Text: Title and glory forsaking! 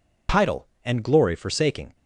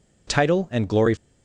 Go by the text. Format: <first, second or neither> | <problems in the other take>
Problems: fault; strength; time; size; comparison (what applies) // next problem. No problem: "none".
first | stops before "forsaking"; at 1.1 s